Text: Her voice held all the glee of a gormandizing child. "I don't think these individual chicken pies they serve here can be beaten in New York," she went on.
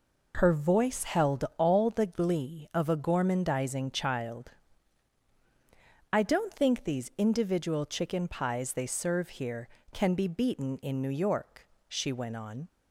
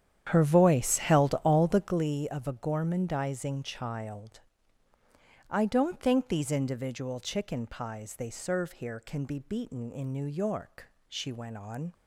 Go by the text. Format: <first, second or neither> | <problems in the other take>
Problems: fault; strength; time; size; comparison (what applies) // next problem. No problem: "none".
first | starts louder than the rest; strong; until 2.0 s; 9.5 dB